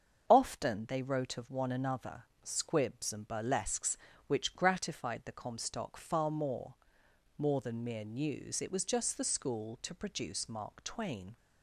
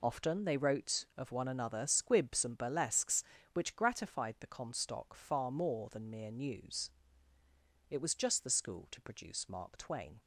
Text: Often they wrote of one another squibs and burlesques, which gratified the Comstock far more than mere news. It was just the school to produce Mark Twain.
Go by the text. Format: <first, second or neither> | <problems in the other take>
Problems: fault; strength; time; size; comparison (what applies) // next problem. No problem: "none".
second | starts louder than the rest; until 1.2 s; 7 dB // pauses between "another" and "squibs"; slight; at 2.2 s; 0.18 s long // says "more" twice; at 7.3 s